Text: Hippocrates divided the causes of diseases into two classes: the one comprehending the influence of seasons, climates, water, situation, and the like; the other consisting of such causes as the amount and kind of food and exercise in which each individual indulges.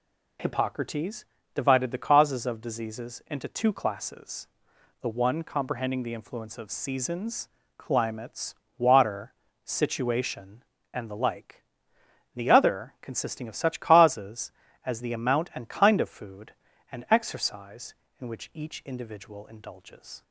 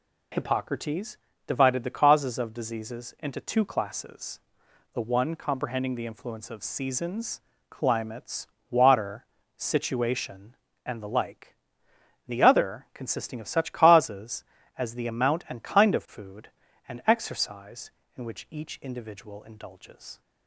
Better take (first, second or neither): neither